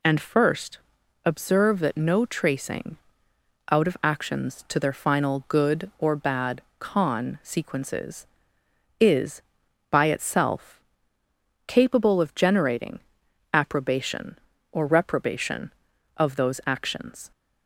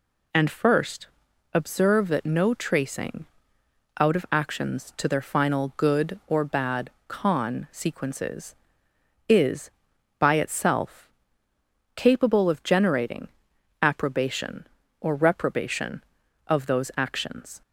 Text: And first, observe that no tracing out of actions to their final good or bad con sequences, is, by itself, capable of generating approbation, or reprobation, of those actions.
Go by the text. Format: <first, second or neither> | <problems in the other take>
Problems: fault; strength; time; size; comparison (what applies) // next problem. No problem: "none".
neither | pauses between "tracing" and "out"; noticeable; the same in both // pauses between "bad" and "con"; slight; the same in both // pauses between "generating" and "approbation"; noticeable; the same in both